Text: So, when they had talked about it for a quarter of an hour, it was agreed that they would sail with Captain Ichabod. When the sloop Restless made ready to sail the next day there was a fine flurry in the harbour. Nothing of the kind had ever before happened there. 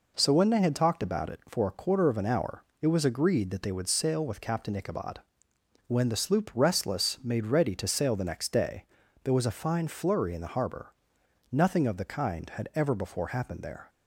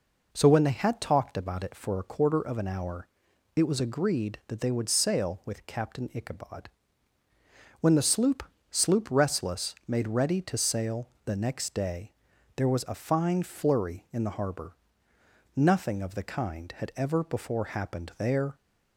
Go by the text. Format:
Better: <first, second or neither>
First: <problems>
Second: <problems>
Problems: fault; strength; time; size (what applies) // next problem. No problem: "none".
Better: first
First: pauses between "day" and "there"; at 8.8 s; 0.38 s long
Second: says "sloop" twice; at 8.6 s // pauses between "sail" and "the"; slight; at 11.0 s; 0.16 s long // pauses between "day" and "there"; at 12.1 s; 0.42 s long